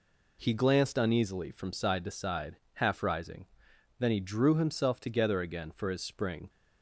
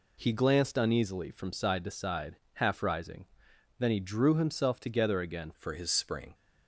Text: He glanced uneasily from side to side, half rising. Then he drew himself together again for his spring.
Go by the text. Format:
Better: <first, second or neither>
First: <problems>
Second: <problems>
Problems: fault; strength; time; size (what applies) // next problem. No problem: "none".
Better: first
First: none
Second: changes voice at "for"; from 5.5 s on; 0.8 s long